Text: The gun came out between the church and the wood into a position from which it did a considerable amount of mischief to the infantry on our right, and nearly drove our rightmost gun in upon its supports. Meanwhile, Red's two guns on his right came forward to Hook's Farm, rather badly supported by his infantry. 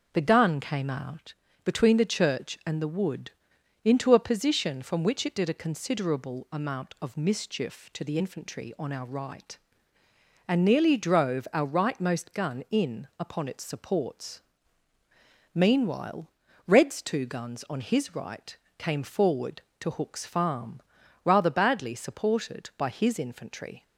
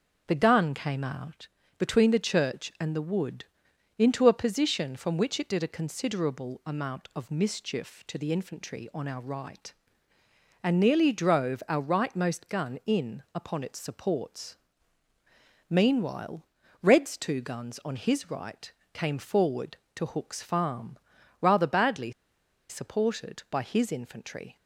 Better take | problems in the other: first | pauses between "out" and "between"; slight; at 1.4 s; 0.30 s long; slight in the first // pauses between "wood" and "into"; noticeable; at 3.4 s; 0.52 s long; noticeable in the first // pauses between "right" and "came"; slight; at 18.7 s; 0.22 s long; slight in the first // pauses between "badly" and "supported"; noticeable; at 22.1 s; 0.57 s long

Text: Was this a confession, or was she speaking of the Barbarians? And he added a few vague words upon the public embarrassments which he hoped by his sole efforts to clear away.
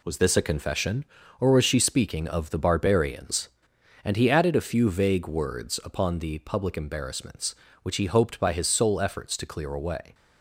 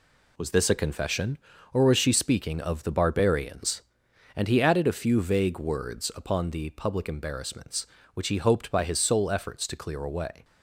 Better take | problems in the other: neither | none

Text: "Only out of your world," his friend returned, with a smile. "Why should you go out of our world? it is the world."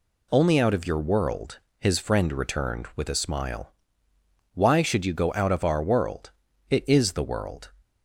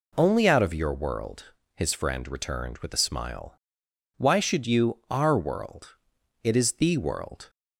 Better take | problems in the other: first | skips "go out of"; at 5.0 s

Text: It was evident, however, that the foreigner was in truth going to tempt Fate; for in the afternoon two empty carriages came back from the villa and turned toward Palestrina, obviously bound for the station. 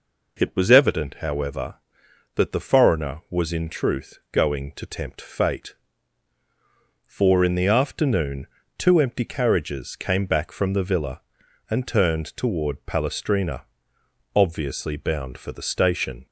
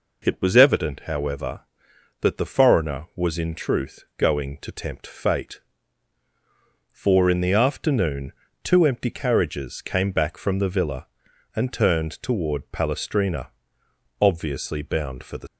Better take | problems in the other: first | pauses between "afternoon" and "two"; slight; at 8.3 s; 0.32 s long; slight in the first // stops before "station"; at 15.4 s

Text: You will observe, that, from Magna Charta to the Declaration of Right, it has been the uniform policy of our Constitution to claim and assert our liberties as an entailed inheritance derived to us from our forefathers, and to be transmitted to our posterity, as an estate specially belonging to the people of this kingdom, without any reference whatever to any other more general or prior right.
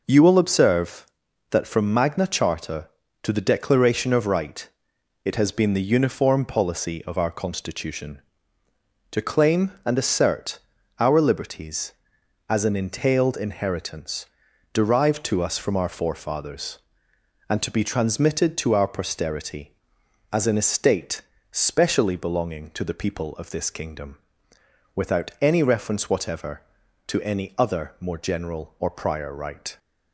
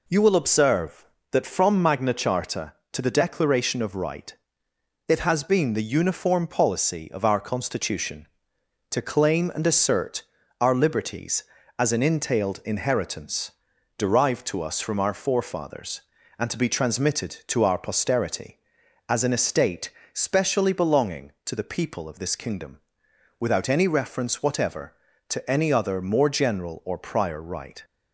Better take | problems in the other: neither | pauses between "assert" and "our"; the same in both // pauses between "inheritance" and "derived"; the same in both // pauses between "estate" and "specially"; slight; the same in both

